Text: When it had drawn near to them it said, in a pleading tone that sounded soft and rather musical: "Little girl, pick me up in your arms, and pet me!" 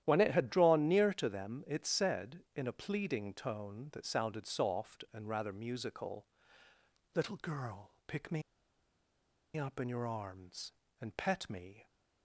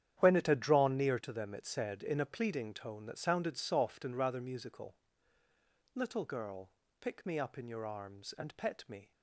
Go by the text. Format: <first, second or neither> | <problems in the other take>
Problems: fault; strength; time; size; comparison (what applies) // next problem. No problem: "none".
second | starts louder than the rest; strong; until 1.0 s; 11.5 dB; strong in the second // pauses between "me" and "up"; at 8.4 s; 1.1 s long